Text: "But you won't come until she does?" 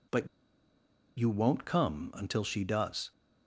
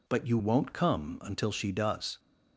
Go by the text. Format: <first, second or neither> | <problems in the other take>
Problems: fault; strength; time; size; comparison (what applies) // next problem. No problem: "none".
second | pauses between "But" and "you"; noticeable; at 0.2 s; 0.91 s long